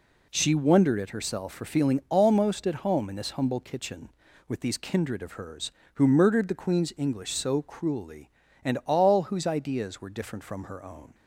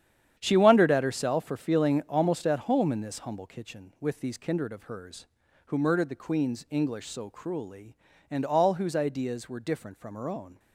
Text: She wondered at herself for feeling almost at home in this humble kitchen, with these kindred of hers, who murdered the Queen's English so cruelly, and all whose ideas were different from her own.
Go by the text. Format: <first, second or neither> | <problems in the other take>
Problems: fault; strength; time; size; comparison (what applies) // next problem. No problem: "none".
first | gets quieter; strong; throughout; 10 dB